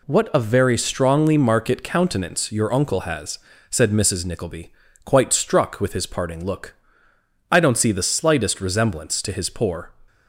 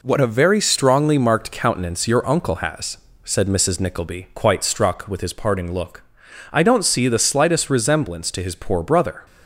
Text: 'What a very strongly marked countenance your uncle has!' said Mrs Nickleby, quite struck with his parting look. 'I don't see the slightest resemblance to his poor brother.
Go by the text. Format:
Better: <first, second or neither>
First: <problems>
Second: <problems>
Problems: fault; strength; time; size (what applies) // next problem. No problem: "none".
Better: second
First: stops before "brother"; at 10.0 s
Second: none